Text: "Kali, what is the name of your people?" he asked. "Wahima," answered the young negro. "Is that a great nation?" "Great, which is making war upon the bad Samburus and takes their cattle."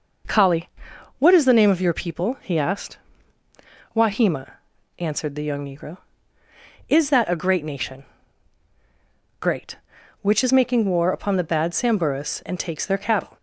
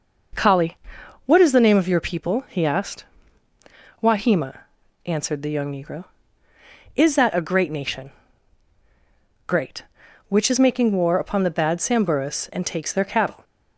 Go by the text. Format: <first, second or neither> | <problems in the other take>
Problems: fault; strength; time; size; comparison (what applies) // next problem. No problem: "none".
neither | none